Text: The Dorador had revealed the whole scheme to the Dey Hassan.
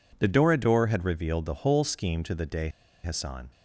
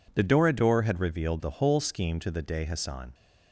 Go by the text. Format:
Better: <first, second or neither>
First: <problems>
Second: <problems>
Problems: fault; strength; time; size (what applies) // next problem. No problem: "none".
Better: second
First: pauses between "Dey" and "Hassan"; slight; at 2.6 s; 0.34 s long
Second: none